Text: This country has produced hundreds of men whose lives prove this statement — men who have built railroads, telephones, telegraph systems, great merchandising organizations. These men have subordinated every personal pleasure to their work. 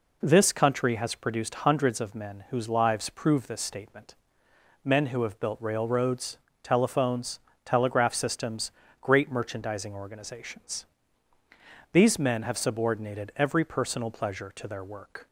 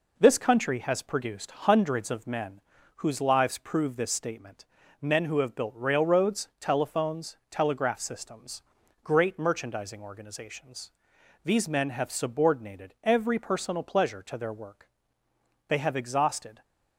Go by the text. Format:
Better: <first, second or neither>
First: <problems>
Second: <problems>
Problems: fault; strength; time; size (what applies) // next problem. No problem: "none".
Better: first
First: none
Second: pauses between "men" and "whose"; slight; at 2.6 s; 0.36 s long // goes on to say "They have exhausted"; noticeable; from 15.6 s on; 0.94 s long